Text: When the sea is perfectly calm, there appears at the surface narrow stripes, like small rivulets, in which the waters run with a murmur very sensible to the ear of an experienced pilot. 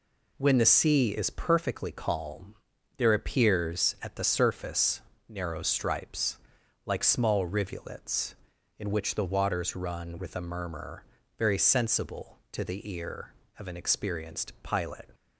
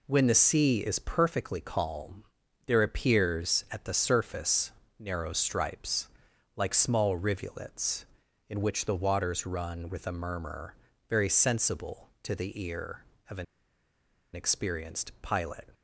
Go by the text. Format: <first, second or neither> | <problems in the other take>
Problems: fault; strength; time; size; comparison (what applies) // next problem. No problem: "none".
first | pauses between "surface" and "narrow"; slight; at 4.6 s; 0.28 s long; slight in the first // pauses between "murmur" and "very"; slight; at 10.7 s; 0.34 s long; slight in the first // pauses between "an" and "experienced"; noticeable; at 13.4 s; 0.91 s long